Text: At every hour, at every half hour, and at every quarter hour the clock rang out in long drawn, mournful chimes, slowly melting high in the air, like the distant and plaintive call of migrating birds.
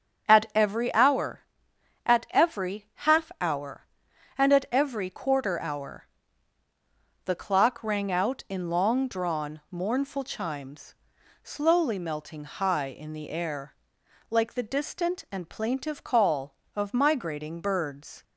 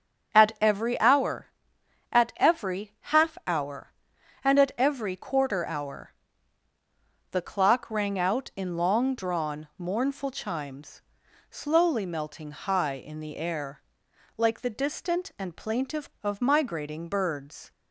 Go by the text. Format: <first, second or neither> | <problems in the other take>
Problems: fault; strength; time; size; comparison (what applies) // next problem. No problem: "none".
first | starts louder than the rest; strong; until 1.3 s; 7.5 dB; strong in the first // pauses between "hour" and "the"; at 6.1 s; 1.1 s long; also in the first // skips "call"; at 16.1 s